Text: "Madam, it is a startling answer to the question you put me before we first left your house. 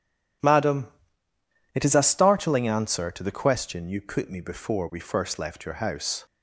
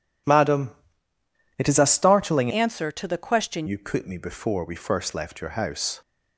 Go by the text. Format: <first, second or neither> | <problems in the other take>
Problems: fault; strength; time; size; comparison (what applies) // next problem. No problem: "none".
first | changes voice from "answer" to "question"; from 2.5 to 3.6 s; 1.1 s long